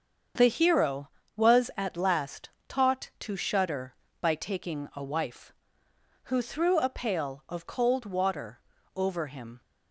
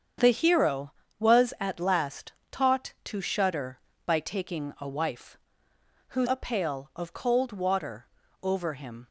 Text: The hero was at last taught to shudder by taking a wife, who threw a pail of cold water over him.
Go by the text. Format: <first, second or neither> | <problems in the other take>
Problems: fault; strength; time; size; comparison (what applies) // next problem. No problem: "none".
first | starts louder than the rest; strong; until 1.4 s; 7.5 dB; also in the first // pauses between "last" and "taught"; slight; at 2.3 s; 0.18 s long; slight in the first // skips "threw"; at 6.2 s // pauses between "water" and "over"; at 8.0 s; 0.38 s long; also in the first